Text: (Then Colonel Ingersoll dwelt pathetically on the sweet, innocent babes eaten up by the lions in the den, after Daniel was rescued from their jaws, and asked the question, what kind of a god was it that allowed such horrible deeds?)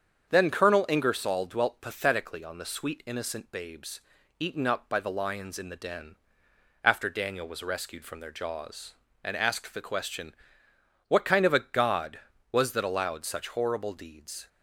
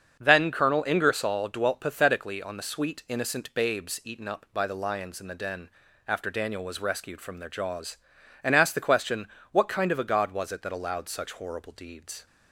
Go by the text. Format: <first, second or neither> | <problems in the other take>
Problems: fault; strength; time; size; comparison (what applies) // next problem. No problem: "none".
second | starts louder than the rest; strong; until 1.3 s; 7.5 dB; also in the second // pauses between "babes" and "eaten"; at 3.9 s; 0.40 s long // skips "it"; at 12.7 s